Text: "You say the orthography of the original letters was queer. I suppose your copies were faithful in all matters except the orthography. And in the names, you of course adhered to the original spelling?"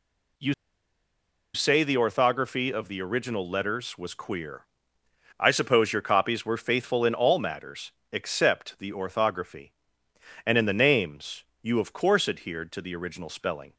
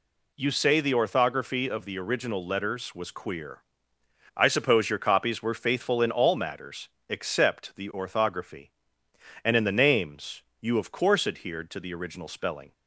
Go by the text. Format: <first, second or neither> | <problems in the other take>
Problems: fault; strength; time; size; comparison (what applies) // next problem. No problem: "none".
second | pauses between "You" and "say"; at 0.5 s; 1.0 s long // pauses between "matters" and "except"; slight; at 7.9 s; 0.18 s long; slight in the second